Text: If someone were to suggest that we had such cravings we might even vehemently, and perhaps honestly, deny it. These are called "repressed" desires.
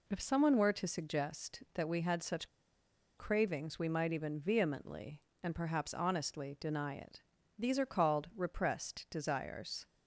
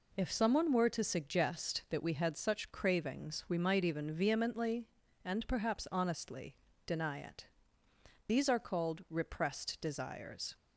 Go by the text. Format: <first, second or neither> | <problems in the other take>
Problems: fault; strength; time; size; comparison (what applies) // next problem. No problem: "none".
second | pauses between "such" and "cravings"; noticeable; at 2.4 s; 0.69 s long